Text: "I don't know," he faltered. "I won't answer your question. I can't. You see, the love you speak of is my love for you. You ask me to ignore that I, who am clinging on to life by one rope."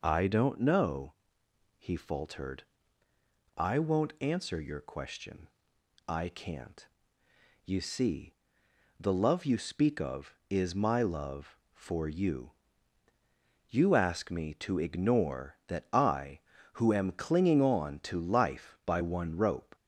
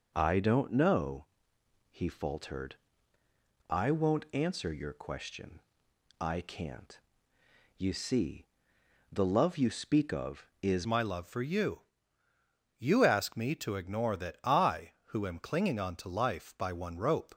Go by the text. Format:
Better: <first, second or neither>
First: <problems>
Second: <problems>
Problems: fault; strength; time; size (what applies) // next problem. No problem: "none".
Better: first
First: none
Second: changes voice at "my"; from 10.8 s on; 6.5 s long